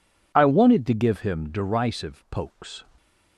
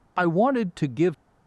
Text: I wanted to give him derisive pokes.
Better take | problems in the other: first | stops before "him derisive pokes"; at 1.1 s

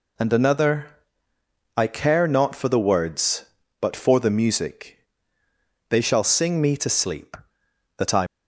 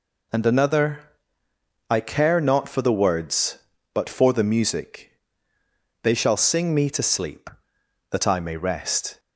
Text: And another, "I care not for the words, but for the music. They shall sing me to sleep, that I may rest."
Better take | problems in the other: second | stops before "may rest"; at 8.2 s

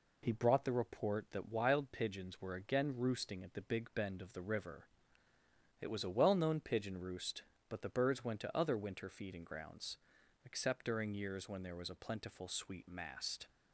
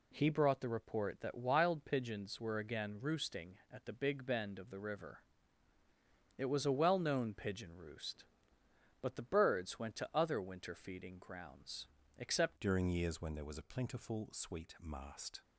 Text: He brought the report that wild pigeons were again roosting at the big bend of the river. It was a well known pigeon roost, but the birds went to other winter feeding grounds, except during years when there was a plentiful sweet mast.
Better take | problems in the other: first | changes voice at "during"; from 12.6 s on; 2.8 s long

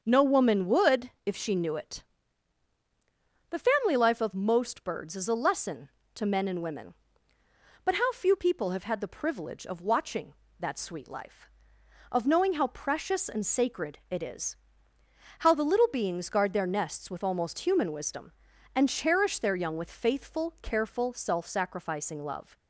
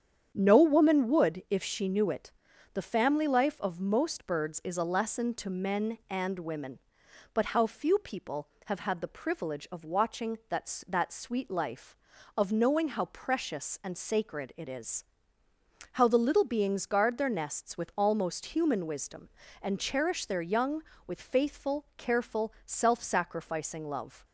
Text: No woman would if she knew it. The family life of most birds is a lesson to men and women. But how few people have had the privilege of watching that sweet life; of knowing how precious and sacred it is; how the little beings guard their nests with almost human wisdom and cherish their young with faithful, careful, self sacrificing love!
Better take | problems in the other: first | starts louder than the rest; strong; until 1.3 s; 8.5 dB; also in the first // says "that" twice; at 10.8 s

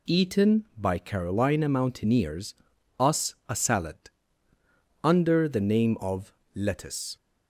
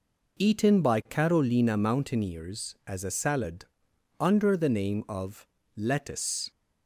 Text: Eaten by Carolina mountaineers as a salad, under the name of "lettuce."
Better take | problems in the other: second | says "us" for "as"; at 2.9 s // pauses between "of" and "lettuce"; slight; at 6.3 s; 0.20 s long; slight in the second

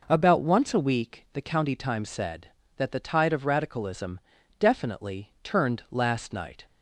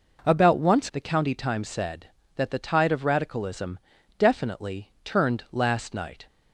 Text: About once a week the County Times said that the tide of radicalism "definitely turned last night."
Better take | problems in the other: first | skips "a week"; at 0.9 s // pauses between "radicalism" and "definitely"; at 3.7 s; 0.40 s long; also in the first

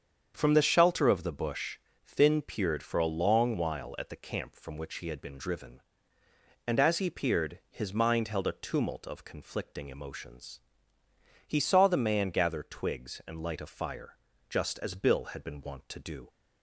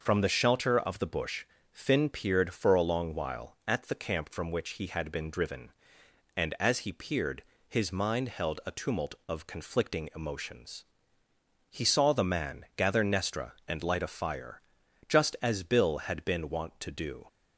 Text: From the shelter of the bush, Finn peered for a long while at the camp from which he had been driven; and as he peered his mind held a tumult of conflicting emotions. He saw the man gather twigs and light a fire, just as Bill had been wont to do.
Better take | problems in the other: first | starts louder than the rest; noticeable; until 1.0 s; 6 dB; strong in the first // pauses between "peered" and "his"; slight; at 7.4 s; 0.24 s long // says "nestra" for "twigs"; at 13.0 s

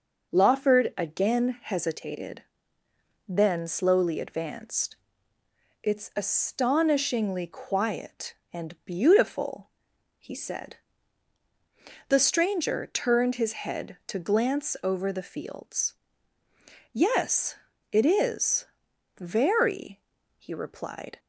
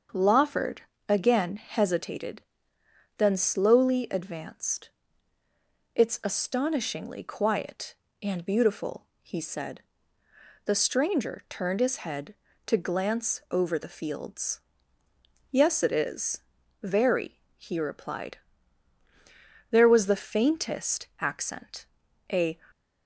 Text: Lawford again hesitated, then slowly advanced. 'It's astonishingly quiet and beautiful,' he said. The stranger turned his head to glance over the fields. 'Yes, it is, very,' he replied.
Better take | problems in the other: first | starts louder than the rest; until 1.3 s; 7 dB // pauses between "Lawford" and "again"; slight; at 0.8 s; 0.26 s long // goes on to say "There was the faintest accent a"; strong; from 19.7 s on; 2.9 s long

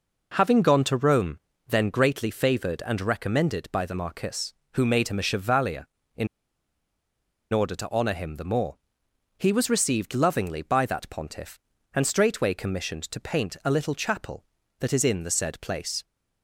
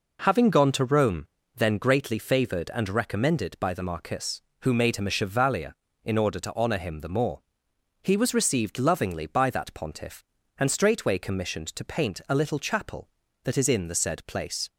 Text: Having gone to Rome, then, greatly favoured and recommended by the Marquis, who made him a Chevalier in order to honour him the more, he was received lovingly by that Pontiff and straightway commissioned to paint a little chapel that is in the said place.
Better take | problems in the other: second | pauses between "in" and "order"; strong; at 6.2 s; 1.2 s long

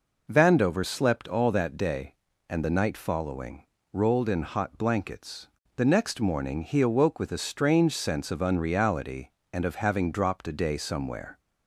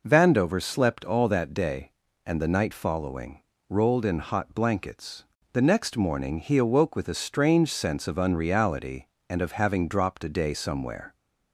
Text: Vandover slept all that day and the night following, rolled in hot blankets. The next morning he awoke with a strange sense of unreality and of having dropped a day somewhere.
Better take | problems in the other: neither | none

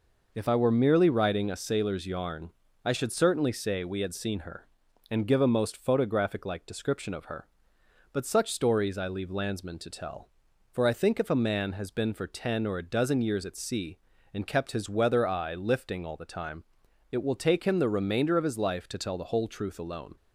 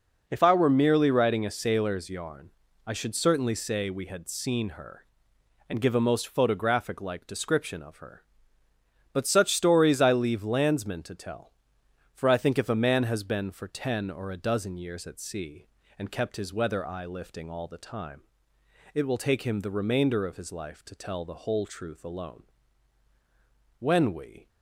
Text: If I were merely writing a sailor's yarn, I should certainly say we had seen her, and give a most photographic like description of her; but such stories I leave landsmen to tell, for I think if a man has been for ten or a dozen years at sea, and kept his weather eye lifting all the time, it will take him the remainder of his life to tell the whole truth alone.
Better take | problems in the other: first | goes on to say "When we"; noticeable; from 23.7 s on; 0.70 s long

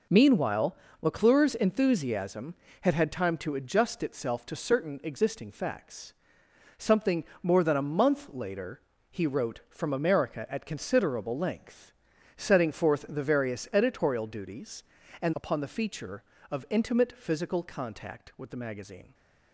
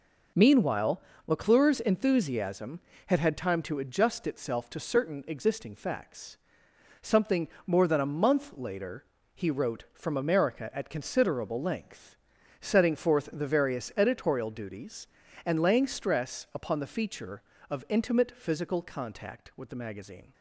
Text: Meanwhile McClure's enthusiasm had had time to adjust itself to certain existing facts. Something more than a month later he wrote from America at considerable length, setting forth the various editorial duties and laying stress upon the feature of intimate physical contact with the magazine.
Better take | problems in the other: second | pauses between "Meanwhile" and "McClure's"; slight; at 0.7 s; 0.26 s long; slight in the second // pauses between "Something" and "more"; slight; at 7.2 s; 0.20 s long; slight in the second // pauses between "later" and "he"; slight; at 8.8 s; 0.30 s long; slight in the second // skips "laying stress"; at 15.3 s

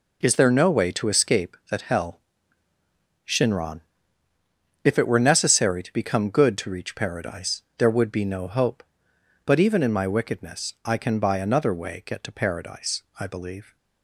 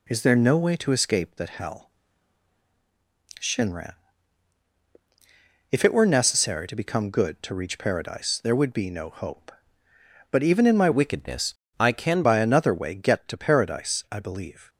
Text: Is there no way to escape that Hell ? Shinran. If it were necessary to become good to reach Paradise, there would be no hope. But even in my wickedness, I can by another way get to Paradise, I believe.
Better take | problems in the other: first | changes voice from "wickedness" to "can"; from 10.9 to 12.2 s; 1.3 s long

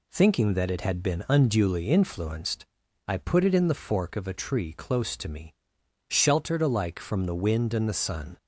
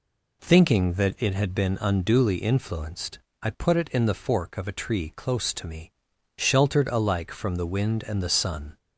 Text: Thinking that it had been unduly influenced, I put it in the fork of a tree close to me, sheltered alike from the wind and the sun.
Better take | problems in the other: neither | none

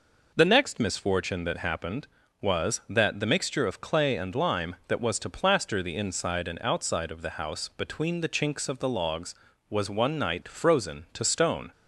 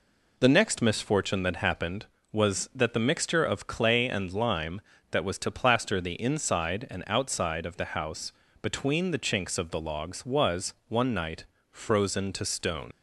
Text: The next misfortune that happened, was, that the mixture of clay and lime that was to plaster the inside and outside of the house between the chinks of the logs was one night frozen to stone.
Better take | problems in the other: first | pauses between "house" and "between"; slight; at 8.3 s; 0.28 s long // pauses between "was" and "one"; slight; at 10.7 s; 0.16 s long // pauses between "night" and "frozen"; slight; at 11.4 s; 0.26 s long // leaves "stone" unfinished; at 12.9 s; 50 ms

